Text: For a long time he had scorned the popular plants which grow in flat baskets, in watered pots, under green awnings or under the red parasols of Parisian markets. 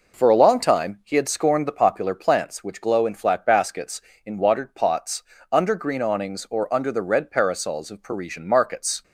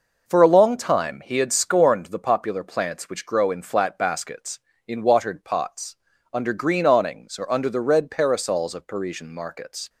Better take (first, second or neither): second